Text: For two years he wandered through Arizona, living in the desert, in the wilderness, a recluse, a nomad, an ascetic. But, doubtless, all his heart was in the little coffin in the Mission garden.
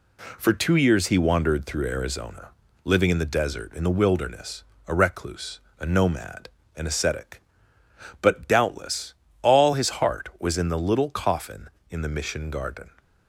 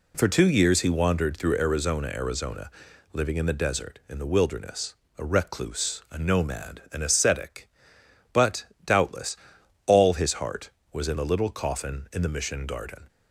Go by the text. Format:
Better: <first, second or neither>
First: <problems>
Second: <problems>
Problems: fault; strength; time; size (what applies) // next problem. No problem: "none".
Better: first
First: none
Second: says "Arizona" twice; at 2.0 s